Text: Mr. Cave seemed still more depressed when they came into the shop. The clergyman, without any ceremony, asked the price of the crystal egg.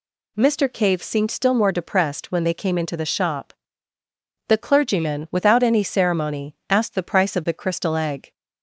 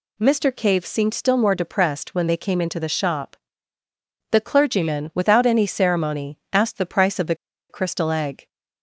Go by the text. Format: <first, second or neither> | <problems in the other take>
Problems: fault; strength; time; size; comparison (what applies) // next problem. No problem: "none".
first | pauses between "the" and "crystal"; slight; at 7.3 s; 0.34 s long